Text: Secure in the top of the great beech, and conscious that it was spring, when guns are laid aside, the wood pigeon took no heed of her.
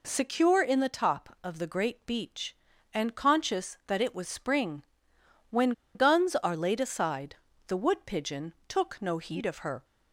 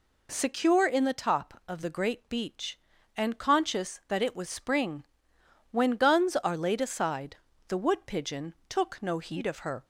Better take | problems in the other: second | pauses between "when" and "guns"; slight; at 5.7 s; 0.23 s long

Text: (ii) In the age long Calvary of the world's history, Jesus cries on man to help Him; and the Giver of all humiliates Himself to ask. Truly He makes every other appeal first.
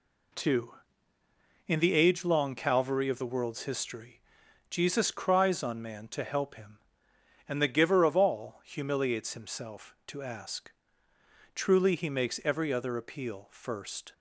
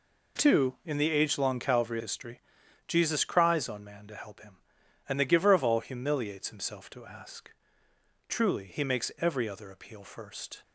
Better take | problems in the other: first | skips "of the world's"; at 1.9 s

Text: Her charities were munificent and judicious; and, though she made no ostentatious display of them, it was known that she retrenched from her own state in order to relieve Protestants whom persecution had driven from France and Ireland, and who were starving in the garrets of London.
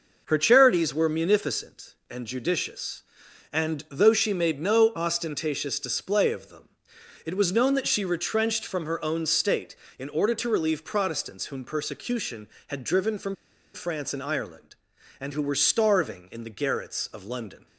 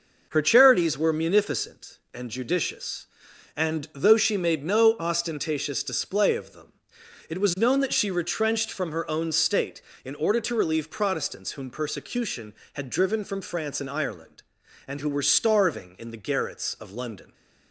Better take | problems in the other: second | pauses between "from" and "France"; at 13.3 s; 0.39 s long

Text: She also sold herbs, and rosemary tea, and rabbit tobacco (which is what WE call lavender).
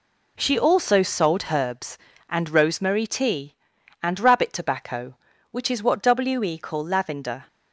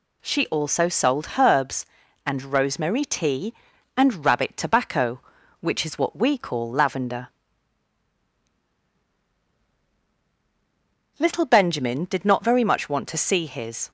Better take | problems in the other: first | goes on to say "LITTLE Benjamin did not very much want to see his"; strong; from 11.1 s on; 2.7 s long

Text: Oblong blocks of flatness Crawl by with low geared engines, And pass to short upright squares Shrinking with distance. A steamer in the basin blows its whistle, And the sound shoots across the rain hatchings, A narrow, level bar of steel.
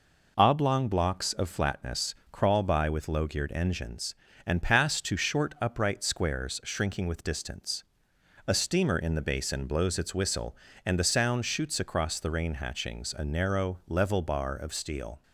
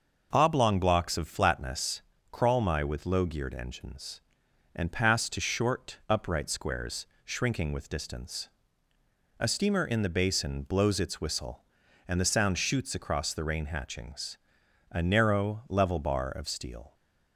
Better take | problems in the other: first | pauses between "flatness" and "Crawl"; slight; at 1.9 s; 0.32 s long; slight in the first // says "my" for "by"; at 2.6 s // pauses between "squares" and "Shrinking"; slight; at 7.0 s; 0.20 s long

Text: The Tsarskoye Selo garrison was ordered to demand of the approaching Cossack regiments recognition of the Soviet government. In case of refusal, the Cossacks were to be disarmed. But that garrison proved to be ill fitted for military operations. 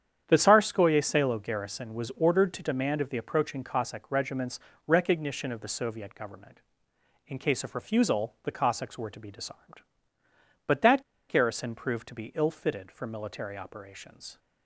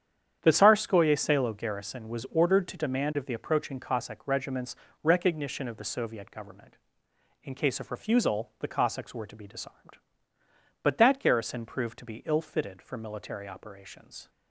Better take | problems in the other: second | starts louder than the rest; strong; until 1.2 s; 9 dB; strong in the second // pauses between "regiments" and "recognition"; slight; at 4.5 s; 0.28 s long; slight in the second // pauses between "that" and "garrison"; slight; at 11.0 s; 0.26 s long

